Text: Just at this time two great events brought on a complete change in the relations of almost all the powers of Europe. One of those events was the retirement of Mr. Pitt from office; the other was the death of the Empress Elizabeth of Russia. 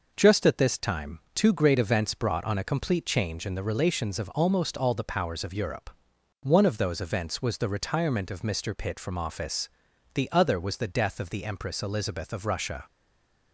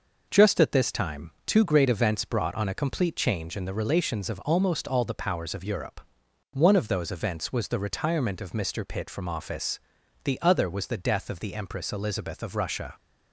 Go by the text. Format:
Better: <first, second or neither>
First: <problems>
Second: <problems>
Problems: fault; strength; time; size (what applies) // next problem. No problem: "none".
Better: second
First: stays silent after the last word; slight; from 12.8 s on; 0.7 s long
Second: none